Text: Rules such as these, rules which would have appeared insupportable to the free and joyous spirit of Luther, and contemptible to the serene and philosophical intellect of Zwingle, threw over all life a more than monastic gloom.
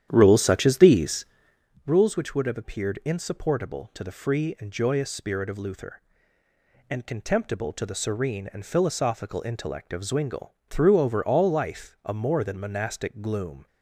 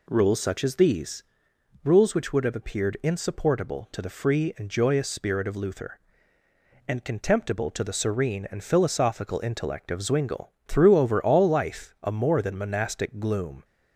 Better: second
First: starts louder than the rest; strong; until 1.8 s; 10.5 dB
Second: none

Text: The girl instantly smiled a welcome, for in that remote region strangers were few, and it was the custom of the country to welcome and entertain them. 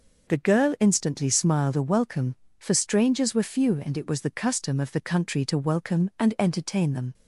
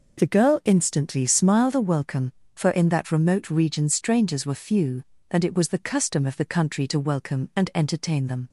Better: second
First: skips "in that remote region"; at 2.7 s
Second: none

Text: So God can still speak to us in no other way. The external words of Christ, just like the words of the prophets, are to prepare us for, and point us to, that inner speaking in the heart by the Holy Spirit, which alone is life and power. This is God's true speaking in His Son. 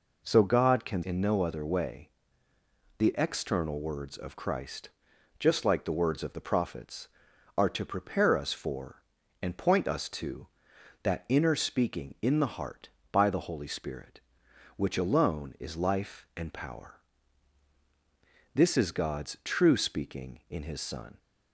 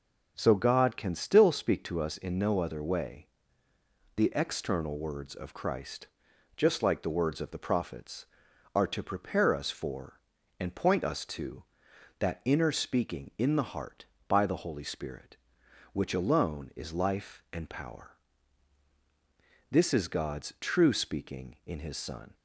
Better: second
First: skips "still speak to us"; at 1.0 s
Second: none

